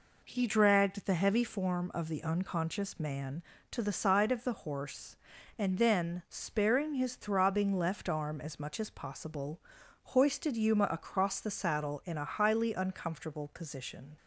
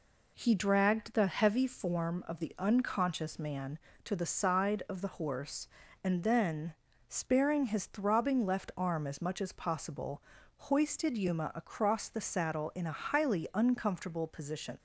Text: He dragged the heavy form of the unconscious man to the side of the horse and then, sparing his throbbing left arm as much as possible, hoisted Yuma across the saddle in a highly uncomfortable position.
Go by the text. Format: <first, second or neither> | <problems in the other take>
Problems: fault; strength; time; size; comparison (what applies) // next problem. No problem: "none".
neither | none